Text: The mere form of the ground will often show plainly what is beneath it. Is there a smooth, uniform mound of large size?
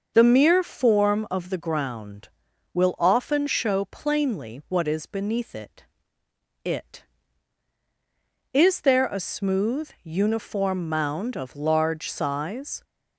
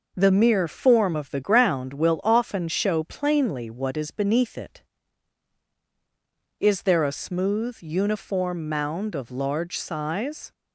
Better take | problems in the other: second | starts louder than the rest; noticeable; until 1.1 s; 6 dB // says "it" twice; at 6.6 s

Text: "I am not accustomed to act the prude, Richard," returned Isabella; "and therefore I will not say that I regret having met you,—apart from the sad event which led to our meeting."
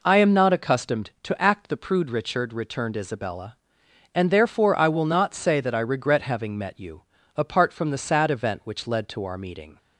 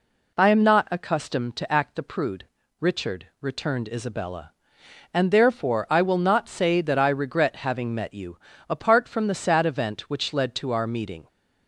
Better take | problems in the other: neither | none

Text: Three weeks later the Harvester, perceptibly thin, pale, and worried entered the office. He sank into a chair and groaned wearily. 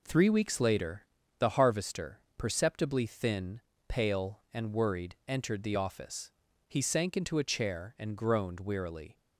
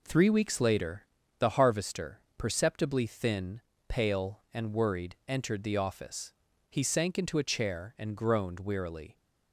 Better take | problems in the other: neither | pauses between "later" and "the"; slight; the same in both

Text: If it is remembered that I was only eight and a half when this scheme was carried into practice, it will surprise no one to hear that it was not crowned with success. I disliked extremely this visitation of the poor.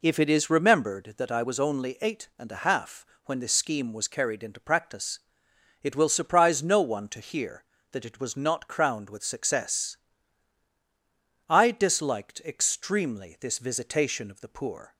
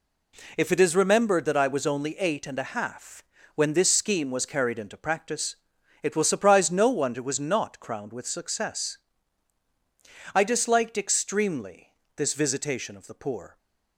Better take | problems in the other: first | pauses between "half" and "when"; slight; at 3.2 s; 0.32 s long; slight in the first // skips "to hear that"; at 7.1 s // pauses between "extremely" and "this"; slight; at 11.9 s; 0.22 s long

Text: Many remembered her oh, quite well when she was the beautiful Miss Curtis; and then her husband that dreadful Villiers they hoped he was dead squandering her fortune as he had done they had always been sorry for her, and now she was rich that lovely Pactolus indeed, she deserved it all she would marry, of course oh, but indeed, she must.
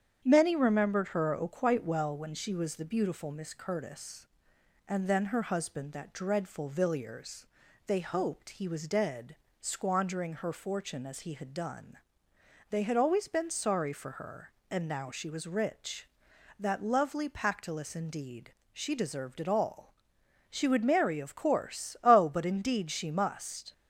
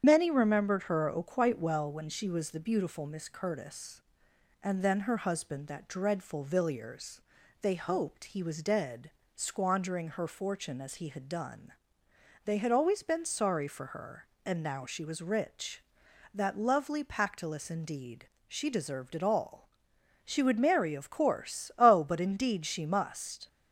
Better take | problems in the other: first | loses the start of "Many"; at 0.0 s; 45 ms // starts louder than the rest; strong; until 1.0 s; 8.5 dB; strong in the first // pauses between "Villiers" and "they"; at 7.1 s; 0.42 s long; also in the first // pauses between "dead" and "squandering"; slight; at 9.0 s; 0.26 s long; slight in the first // pauses between "done" and "they"; noticeable; at 11.7 s; 0.74 s long; noticeable in the first // pauses between "all" and "she"; noticeable; at 19.6 s; 0.56 s long; noticeable in the first

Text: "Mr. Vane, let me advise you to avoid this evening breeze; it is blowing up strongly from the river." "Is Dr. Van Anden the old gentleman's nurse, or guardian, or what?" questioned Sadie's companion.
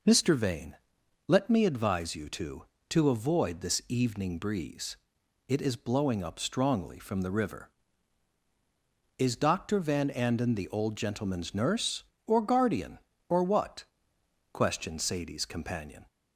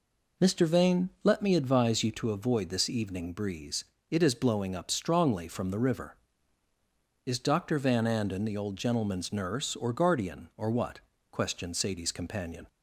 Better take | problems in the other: second | says "to" twice; at 2.8 s

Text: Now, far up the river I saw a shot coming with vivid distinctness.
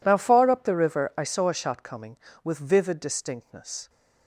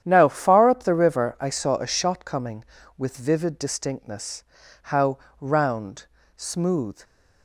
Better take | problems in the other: first | starts louder than the rest; strong; until 1.0 s; 10 dB // goes on to say "How round smooth"; strong; from 4.8 s on; 2.1 s long

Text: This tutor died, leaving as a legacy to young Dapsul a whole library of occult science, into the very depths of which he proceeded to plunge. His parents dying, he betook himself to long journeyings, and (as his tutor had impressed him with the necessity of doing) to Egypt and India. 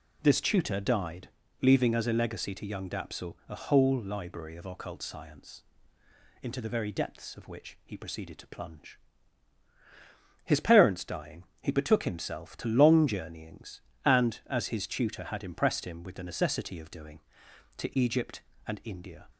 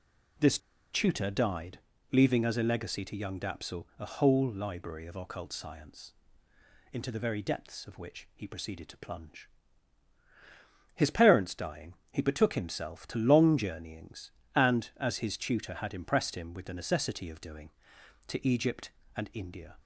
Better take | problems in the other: first | pauses between "This" and "tutor"; slight; at 0.5 s; 0.34 s long

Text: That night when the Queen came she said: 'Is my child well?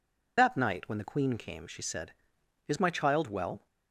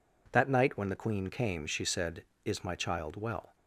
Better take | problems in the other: second | loses the start of "That"; at 0.3 s; 60 ms

